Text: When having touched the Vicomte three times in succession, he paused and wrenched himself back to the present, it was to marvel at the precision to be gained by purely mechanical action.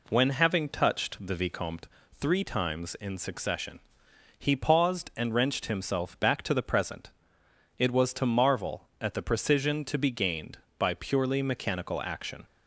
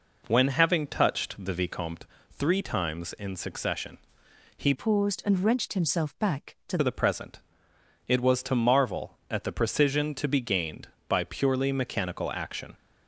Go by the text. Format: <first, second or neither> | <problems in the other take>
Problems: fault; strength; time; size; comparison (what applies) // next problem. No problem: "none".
first | pauses between "Vicomte" and "three"; slight; at 2.0 s; 0.26 s long; slight in the first // changes voice from "paused" to "to"; from 4.7 to 6.7 s; 2.0 s long